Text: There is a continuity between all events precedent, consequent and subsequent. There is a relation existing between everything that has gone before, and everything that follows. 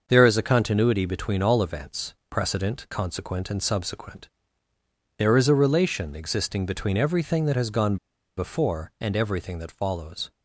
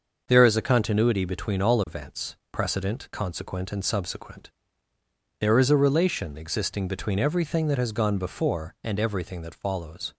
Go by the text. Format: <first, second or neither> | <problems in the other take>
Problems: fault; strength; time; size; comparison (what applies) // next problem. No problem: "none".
second | starts louder than the rest; until 1.0 s; 6.5 dB; also in the second // pauses between "events" and "precedent"; slight; at 2.1 s; 0.16 s long; slight in the second // pauses between "gone" and "before"; at 7.9 s; 0.41 s long